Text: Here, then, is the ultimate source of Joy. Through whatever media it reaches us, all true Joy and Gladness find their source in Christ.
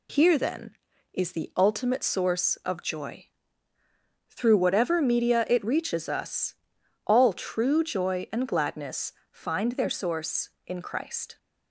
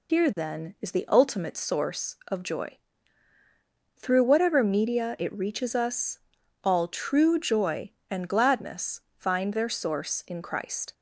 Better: first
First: pauses between "Gladness" and "find"; slight; at 9.1 s; 0.20 s long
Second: loses the start of "Here"; at 0.0 s; 85 ms // pauses between "Gladness" and "find"; slight; at 9.0 s; 0.16 s long

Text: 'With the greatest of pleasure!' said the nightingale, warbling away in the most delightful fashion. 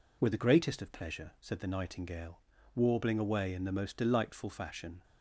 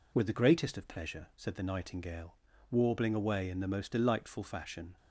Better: neither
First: none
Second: none

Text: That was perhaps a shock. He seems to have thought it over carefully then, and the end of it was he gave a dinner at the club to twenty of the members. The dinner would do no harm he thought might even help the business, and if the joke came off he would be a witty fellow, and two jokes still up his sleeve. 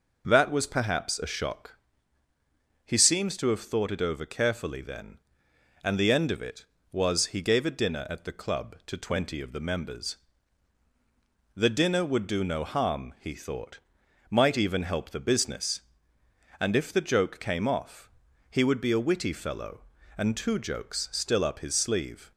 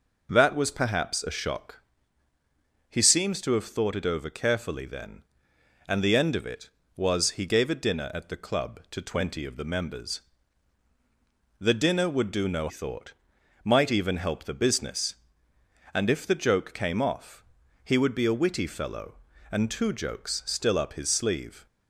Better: first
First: pauses between "thought" and "might"; noticeable; at 13.7 s; 0.50 s long // pauses between "off" and "he"; at 18.0 s; 0.40 s long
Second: skips "harm he"; at 12.6 s // pauses between "thought" and "might"; noticeable; at 13.1 s; 0.50 s long // pauses between "off" and "he"; at 17.4 s; 0.40 s long

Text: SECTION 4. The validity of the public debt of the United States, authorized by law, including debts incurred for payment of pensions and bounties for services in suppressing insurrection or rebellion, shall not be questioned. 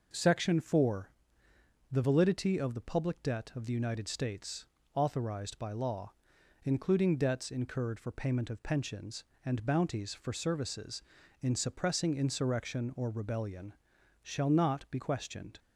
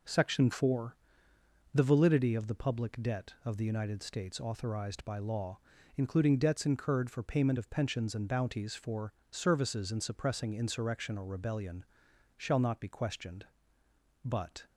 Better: first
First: none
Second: pauses between "for" and "services"; slight; at 9.1 s; 0.18 s long // goes on to say "But"; slight; from 14.2 s on; 0.40 s long

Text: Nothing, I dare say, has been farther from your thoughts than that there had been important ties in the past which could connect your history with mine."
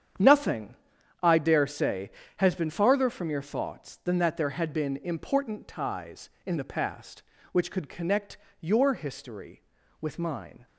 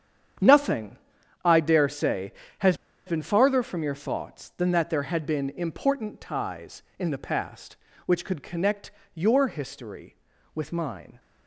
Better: first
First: starts louder than the rest; strong; until 1.6 s; 8.5 dB // pauses between "connect" and "your"; slight; at 8.3 s; 0.22 s long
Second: starts louder than the rest; strong; until 1.8 s; 8.5 dB // pauses between "has" and "been"; slight; at 2.7 s; 0.30 s long // pauses between "connect" and "your"; slight; at 8.9 s; 0.22 s long

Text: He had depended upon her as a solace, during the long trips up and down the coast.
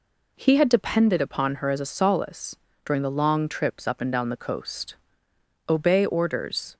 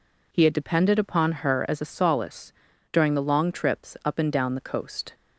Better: second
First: goes on to say "Obey orders"; noticeable; from 5.6 s on; 1.0 s long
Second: none

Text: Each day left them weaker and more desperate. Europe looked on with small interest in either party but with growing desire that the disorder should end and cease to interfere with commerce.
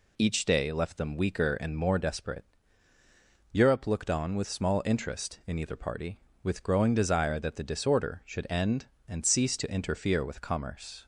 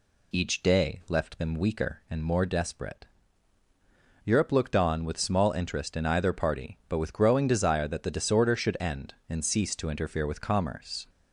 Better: second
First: skips "but"; at 6.3 s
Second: none

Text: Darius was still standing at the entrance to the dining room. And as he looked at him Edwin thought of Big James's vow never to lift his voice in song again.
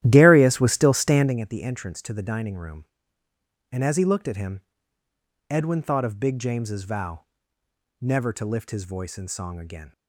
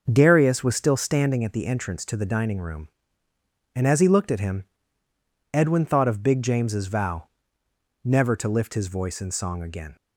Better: second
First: starts louder than the rest; strong; until 1.4 s; 12.5 dB // pauses between "him" and "Edwin"; noticeable; at 4.6 s; 0.86 s long // pauses between "vow" and "never"; noticeable; at 7.2 s; 0.76 s long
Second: pauses between "him" and "Edwin"; noticeable; at 4.6 s; 0.86 s long // pauses between "vow" and "never"; noticeable; at 7.2 s; 0.76 s long

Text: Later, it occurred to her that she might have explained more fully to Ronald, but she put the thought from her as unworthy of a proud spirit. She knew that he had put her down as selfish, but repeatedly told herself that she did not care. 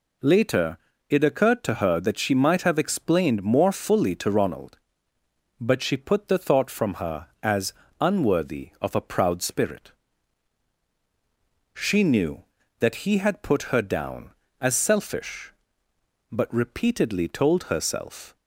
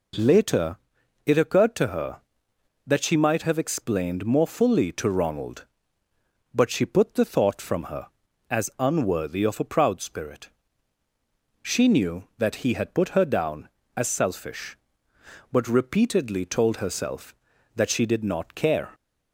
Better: second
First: pauses between "as" and "unworthy"; slight; at 7.7 s; 0.28 s long // stops before "that she did not care"; at 18.3 s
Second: none

